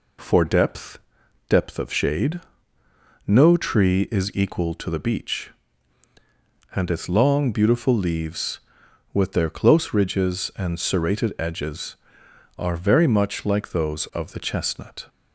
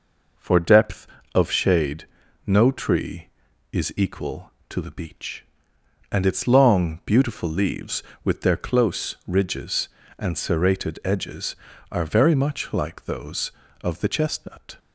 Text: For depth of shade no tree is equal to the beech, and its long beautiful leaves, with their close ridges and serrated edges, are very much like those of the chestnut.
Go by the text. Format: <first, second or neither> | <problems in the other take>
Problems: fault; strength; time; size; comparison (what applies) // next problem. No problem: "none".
second | says "depth" twice; at 1.4 s // pauses between "shade" and "no"; noticeable; at 2.4 s; 0.84 s long; also in the second